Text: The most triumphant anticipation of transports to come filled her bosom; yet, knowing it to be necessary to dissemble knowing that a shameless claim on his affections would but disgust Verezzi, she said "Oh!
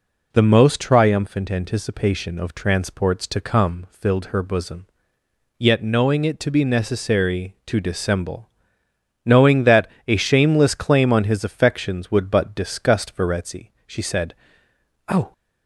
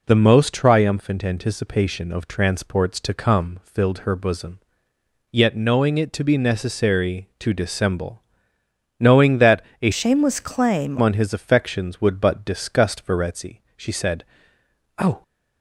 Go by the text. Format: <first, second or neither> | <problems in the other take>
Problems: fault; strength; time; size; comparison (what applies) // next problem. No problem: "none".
first | pauses between "dissemble" and "knowing"; noticeable; at 8.2 s; 0.78 s long; noticeable in the first // pauses between "that" and "a"; slight; at 9.6 s; 0.20 s long; slight in the first // changes voice from "shameless" to "claim"; from 9.9 to 10.9 s; 1.0 s long // pauses between "said" and "Oh"; noticeable; at 14.2 s; 0.74 s long; noticeable in the first